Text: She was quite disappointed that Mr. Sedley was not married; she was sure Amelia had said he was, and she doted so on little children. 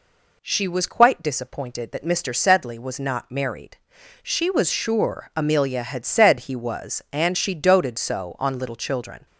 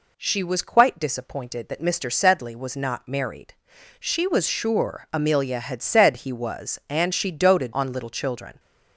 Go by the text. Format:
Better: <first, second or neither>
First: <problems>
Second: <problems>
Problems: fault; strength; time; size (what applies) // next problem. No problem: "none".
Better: first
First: none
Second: skips "so"; at 7.7 s